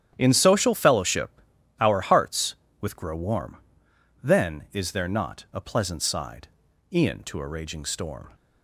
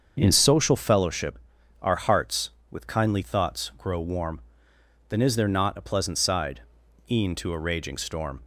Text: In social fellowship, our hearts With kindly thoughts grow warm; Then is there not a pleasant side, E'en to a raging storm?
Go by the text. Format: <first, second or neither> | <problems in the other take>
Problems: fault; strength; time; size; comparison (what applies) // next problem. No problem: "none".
second | starts louder than the rest; strong; until 1.1 s; 10.5 dB; also in the second // skips "kindly thoughts"; at 2.9 s